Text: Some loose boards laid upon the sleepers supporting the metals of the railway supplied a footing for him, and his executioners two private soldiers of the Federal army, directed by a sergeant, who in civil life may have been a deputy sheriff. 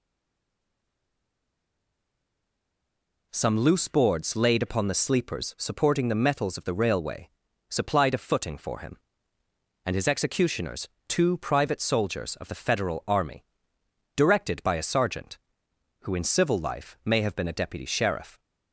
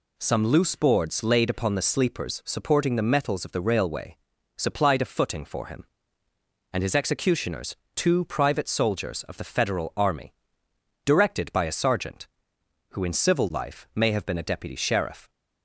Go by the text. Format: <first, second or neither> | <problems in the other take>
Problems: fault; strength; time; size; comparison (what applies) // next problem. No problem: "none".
second | stays silent before the first word; strong; until 3.3 s; 3.3 s long // pauses between "railway" and "supplied"; at 7.2 s; 0.40 s long; also in the second // pauses between "executioners" and "two"; slight; at 10.8 s; 0.18 s long; slight in the second